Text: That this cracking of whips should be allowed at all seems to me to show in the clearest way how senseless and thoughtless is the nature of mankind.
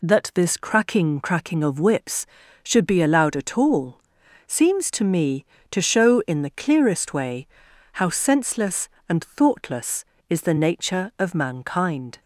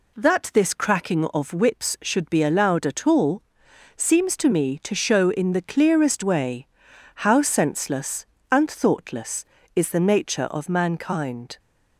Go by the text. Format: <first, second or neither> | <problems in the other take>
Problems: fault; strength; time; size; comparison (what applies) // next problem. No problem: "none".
second | says "cracking" twice; at 1.1 s // pauses between "all" and "seems"; noticeable; at 3.9 s; 0.48 s long; noticeable in the second // pauses between "way" and "how"; noticeable; at 7.4 s; 0.48 s long; noticeable in the second